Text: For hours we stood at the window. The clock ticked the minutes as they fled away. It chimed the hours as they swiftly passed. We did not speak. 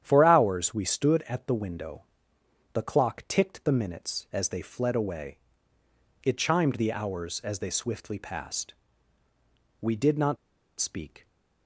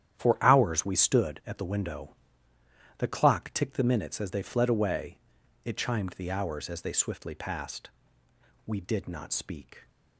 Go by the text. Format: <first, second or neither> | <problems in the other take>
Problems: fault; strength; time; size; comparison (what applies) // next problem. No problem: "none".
second | starts louder than the rest; strong; until 1.0 s; 10 dB; strong in the second // pauses between "not" and "speak"; at 10.3 s; 0.41 s long